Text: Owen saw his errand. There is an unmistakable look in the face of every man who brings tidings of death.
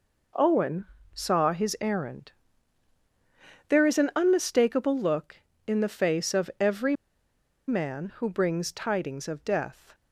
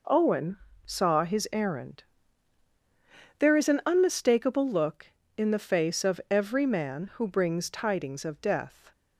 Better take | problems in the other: second | pauses between "Owen" and "saw"; slight; at 0.8 s; 0.28 s long; slight in the second // pauses between "every" and "man"; noticeable; at 6.9 s; 0.72 s long

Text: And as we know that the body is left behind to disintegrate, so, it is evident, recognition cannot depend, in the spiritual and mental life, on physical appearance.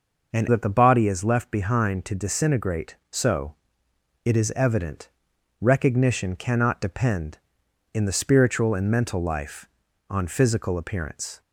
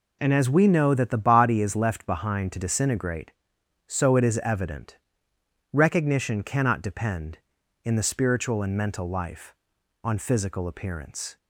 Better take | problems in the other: second | skips "as we know"; at 0.4 s

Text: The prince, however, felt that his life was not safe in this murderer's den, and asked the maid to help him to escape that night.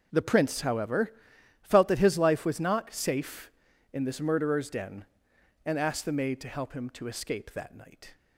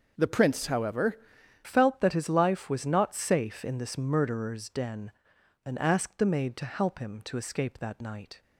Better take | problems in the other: first | changes voice at "felt"; from 1.6 s on; 6.8 s long

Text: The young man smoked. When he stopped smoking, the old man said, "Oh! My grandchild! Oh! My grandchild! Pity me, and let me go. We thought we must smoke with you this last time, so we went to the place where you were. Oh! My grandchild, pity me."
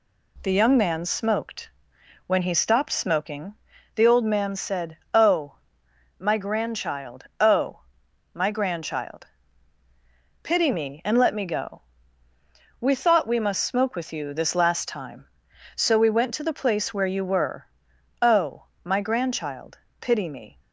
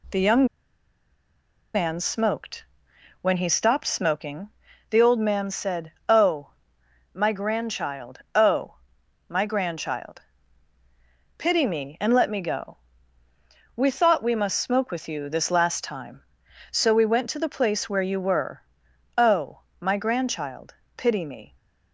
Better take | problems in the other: first | pauses between "young" and "man"; strong; at 0.4 s; 1.2 s long

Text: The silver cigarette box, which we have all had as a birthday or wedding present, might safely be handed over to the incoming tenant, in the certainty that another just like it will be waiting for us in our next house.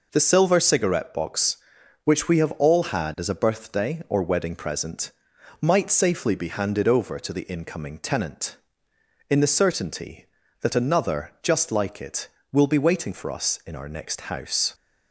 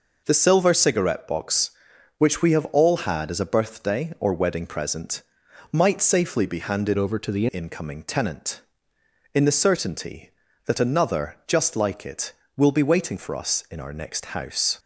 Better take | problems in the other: first | changes voice from "over" to "the"; from 6.9 to 7.4 s; 0.5 s long

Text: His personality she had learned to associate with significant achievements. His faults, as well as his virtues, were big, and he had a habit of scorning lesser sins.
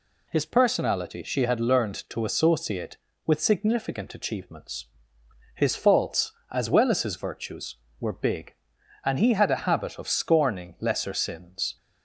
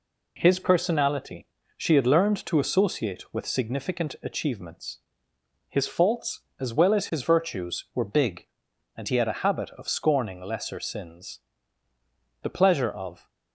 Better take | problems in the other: first | pauses between "personality" and "she"; slight; at 1.4 s; 0.30 s long // goes on to say "The pleasure of"; noticeable; from 12.4 s on; 0.86 s long

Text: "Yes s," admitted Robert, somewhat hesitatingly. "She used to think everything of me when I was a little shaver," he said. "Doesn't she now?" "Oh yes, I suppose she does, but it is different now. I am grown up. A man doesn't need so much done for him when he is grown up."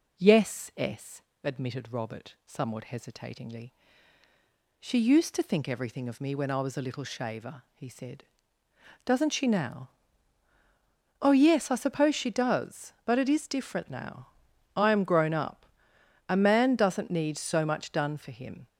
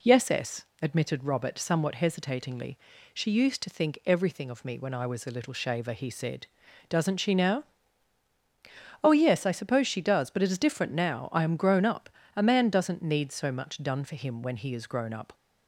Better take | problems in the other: second | stops before "when he is grown up"; at 18.6 s

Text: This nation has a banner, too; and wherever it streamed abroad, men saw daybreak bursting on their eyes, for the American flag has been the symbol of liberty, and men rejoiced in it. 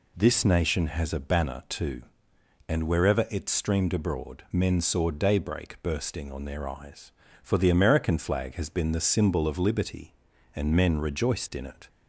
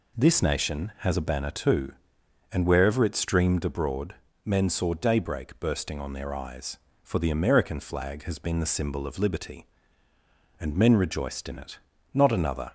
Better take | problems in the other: first | goes on to say "Not another"; from 12.1 s on; 0.60 s long

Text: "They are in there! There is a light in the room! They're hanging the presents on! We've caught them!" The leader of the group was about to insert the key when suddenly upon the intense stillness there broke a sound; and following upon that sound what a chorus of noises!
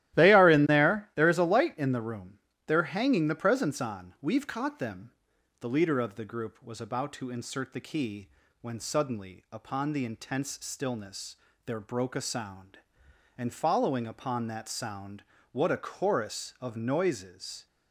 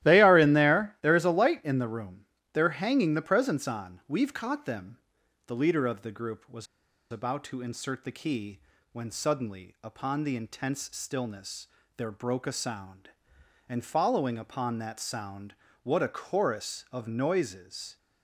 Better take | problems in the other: first | starts louder than the rest; strong; until 1.0 s; 14 dB; strong in the first // pauses between "was" and "about"; at 6.6 s; 0.45 s long // pauses between "key" and "when"; slight; at 8.6 s; 0.32 s long; slight in the first // pauses between "stillness" and "there"; slight; at 11.6 s; 0.30 s long; slight in the first // pauses between "sound" and "what"; slight; at 15.5 s; 0.30 s long; slight in the first

